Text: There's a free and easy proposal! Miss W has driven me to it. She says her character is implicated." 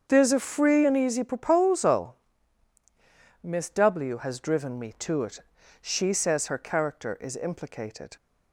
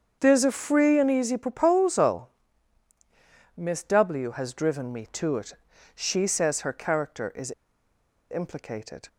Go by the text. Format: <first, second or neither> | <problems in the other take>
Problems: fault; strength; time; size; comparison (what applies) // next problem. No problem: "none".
first | starts louder than the rest; strong; until 1.2 s; 7 dB; also in the first // pauses between "is" and "implicated"; noticeable; at 7.5 s; 0.79 s long